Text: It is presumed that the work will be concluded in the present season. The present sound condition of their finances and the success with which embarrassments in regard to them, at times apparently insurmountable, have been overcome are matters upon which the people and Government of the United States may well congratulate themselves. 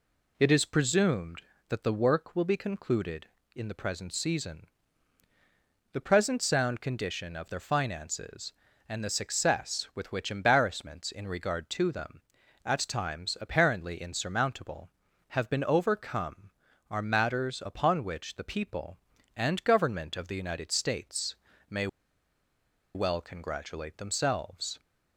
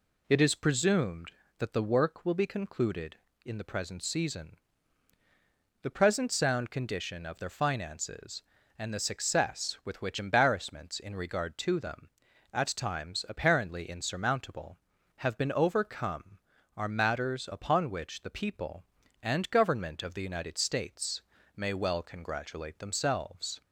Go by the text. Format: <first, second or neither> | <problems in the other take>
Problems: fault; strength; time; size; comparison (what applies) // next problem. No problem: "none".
second | pauses between "States" and "may"; slight; at 21.3 s; 0.32 s long; slight in the second // pauses between "may" and "well"; at 21.8 s; 1.0 s long